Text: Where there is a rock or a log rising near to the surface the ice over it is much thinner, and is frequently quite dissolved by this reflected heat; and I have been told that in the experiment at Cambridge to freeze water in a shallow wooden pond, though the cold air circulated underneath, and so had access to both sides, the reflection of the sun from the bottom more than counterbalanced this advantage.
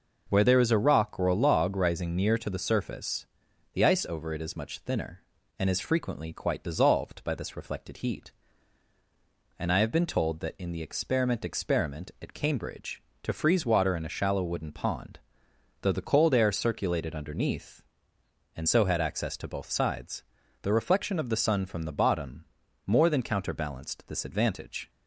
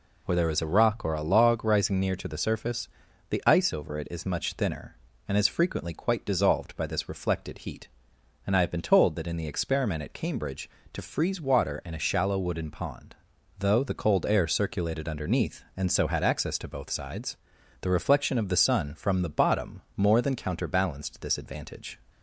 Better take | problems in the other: second | pauses between "surface" and "the"; noticeable; at 3.2 s; 0.46 s long; also in the second // says "experiment" twice; at 11.4 s // pauses between "bottom" and "more"; at 22.4 s; 0.42 s long

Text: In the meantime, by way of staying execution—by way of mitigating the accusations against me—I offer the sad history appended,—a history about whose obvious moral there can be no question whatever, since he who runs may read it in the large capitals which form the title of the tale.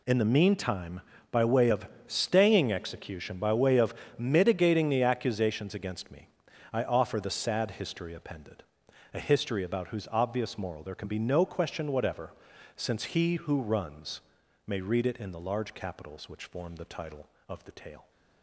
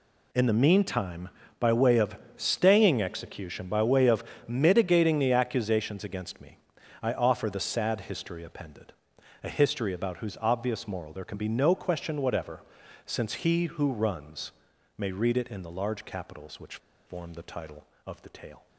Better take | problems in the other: first | pauses between "of" and "staying"; slight; at 2.1 s; 0.22 s long; slight in the first // pauses between "of" and "mitigating"; slight; at 4.2 s; 0.24 s long; slight in the first // pauses between "runs" and "may"; noticeable; at 14.5 s; 0.46 s long; noticeable in the first // pauses between "which" and "form"; slight; at 16.7 s; 0.29 s long

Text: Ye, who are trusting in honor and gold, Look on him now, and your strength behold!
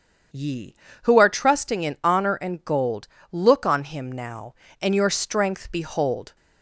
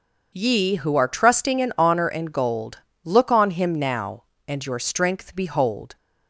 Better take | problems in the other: neither | starts louder than the rest; the same in both

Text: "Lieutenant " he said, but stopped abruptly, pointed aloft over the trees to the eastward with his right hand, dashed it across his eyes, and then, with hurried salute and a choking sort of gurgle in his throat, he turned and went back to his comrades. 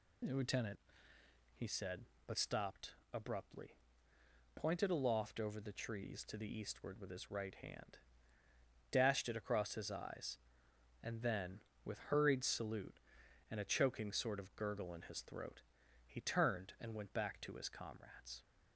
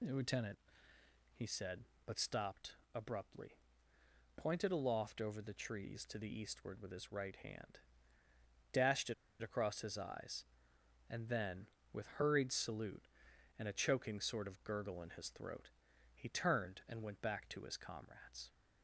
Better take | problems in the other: first | pauses between "stopped" and "abruptly"; slight; at 2.7 s; 0.18 s long; slight in the first // pauses between "it" and "across"; slight; at 9.1 s; 0.27 s long

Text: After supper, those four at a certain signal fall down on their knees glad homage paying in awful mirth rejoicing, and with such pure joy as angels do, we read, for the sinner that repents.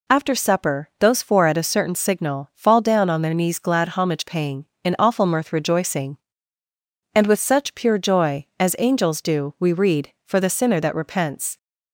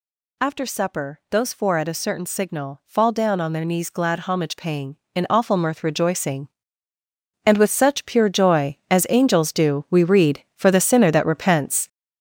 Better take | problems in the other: first | gets louder; strong; throughout; 8.5 dB

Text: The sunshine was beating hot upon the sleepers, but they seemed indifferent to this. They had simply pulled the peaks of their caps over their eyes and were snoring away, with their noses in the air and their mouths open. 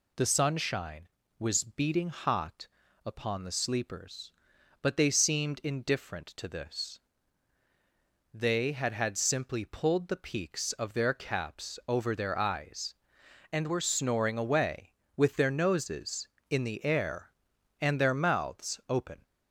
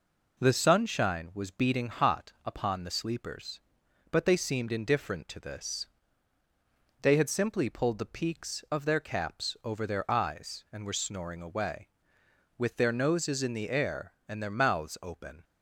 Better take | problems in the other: second | pauses between "hot" and "upon"; slight; at 2.6 s; 0.36 s long // says "had" twice; at 8.9 s

